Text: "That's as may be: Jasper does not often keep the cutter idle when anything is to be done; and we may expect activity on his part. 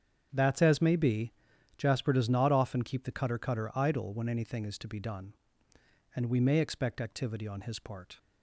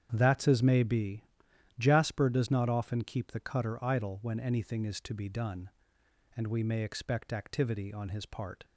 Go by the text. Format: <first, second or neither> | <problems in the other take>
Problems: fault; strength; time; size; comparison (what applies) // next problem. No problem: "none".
second | starts louder than the rest; strong; until 1.3 s; 8 dB; strong in the second // says "cutter" twice; at 3.3 s